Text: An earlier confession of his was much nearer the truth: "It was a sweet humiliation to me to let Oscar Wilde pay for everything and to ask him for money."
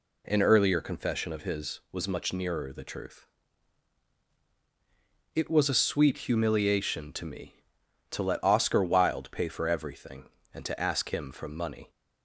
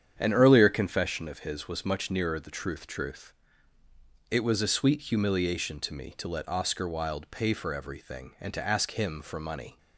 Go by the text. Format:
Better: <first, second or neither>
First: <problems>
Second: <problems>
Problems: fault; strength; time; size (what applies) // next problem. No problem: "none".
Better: first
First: none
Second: starts louder than the rest; strong; until 1.2 s; 8.5 dB // says "truth" twice; at 2.8 s